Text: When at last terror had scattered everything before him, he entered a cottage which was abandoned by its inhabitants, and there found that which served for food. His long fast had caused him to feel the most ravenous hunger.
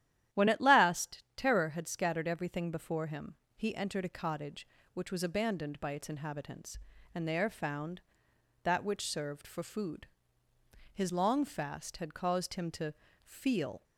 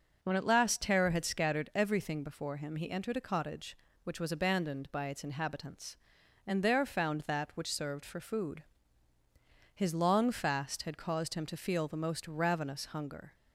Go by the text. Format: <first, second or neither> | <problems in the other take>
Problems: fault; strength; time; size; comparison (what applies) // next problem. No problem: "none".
second | starts louder than the rest; strong; until 1.4 s; 11.5 dB // pauses between "to" and "feel"; slight; at 12.9 s; 0.30 s long // stops before "the most ravenous hunger"; at 13.8 s